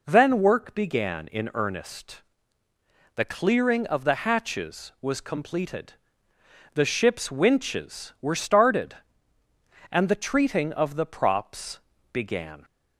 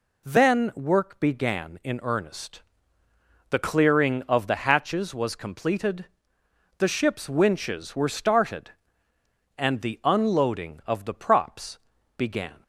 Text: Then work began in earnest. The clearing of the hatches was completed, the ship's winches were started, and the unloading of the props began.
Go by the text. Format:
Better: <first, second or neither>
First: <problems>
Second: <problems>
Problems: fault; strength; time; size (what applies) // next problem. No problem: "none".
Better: second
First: says "treating" for "unloading"; at 10.1 s // pauses between "props" and "began"; slight; at 11.7 s; 0.32 s long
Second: pauses between "props" and "began"; at 11.7 s; 0.38 s long